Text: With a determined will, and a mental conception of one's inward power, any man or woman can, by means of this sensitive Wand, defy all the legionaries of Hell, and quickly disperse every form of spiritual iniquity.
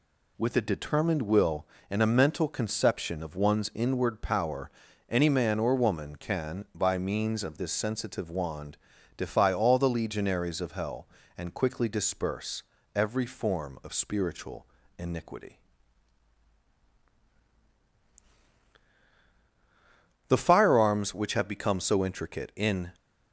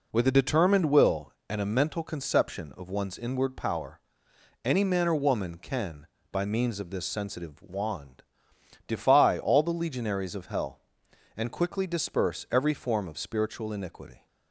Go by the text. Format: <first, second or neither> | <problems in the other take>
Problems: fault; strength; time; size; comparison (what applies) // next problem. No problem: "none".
second | pauses between "disperse" and "every"; slight; at 12.6 s; 0.34 s long // pauses between "spiritual" and "iniquity"; slight; at 14.6 s; 0.34 s long // goes on to say "The firearms which have become so intricate in"; strong; from 20.2 s on; 2.6 s long